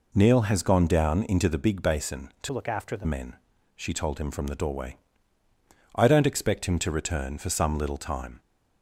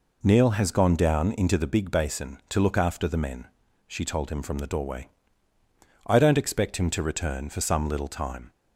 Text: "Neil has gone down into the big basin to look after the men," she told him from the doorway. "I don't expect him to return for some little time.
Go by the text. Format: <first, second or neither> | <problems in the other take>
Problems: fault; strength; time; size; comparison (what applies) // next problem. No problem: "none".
second | changes voice from "look" to "the"; from 2.5 to 3.0 s; 0.5 s long